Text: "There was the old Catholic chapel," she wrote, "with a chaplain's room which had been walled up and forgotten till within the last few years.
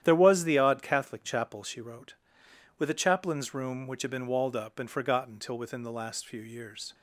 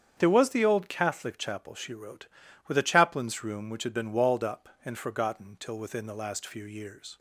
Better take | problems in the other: second | starts louder than the rest; strong; until 1.0 s; 11 dB; strong in the second // says "odd" for "old"; at 0.5 s

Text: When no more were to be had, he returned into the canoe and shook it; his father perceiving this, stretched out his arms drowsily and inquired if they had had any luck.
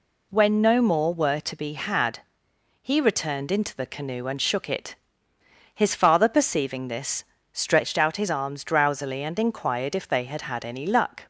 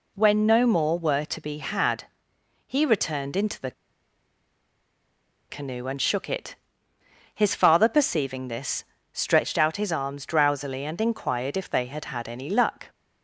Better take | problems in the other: first | pauses between "the" and "canoe"; strong; at 3.7 s; 1.7 s long

